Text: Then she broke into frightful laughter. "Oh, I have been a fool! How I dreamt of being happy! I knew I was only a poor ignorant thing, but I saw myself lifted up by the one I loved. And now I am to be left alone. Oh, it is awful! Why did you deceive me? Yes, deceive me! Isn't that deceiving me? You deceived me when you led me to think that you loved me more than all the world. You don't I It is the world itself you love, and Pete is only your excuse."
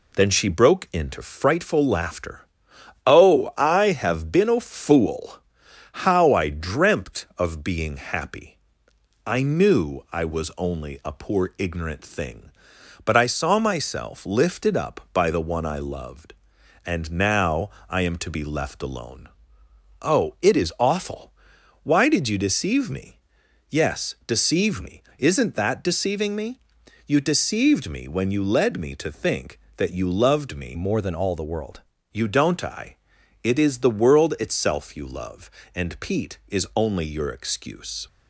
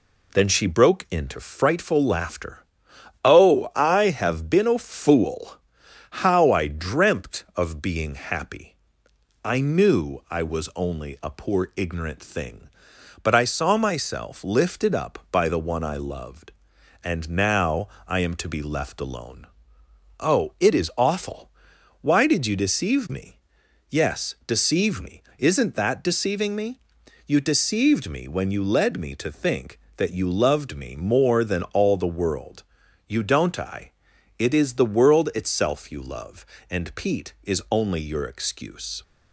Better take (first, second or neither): second